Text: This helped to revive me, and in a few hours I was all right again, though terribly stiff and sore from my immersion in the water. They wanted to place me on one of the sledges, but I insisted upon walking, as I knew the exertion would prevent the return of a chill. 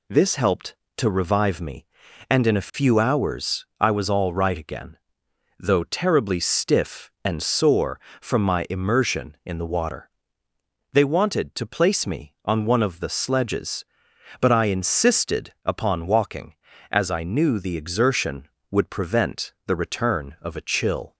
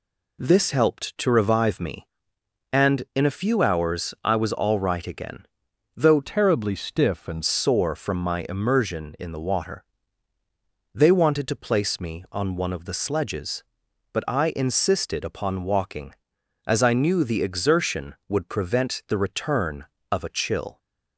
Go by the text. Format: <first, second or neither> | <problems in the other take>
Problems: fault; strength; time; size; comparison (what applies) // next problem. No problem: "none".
first | changes voice from "terribly" to "and"; from 6.2 to 7.4 s; 1.2 s long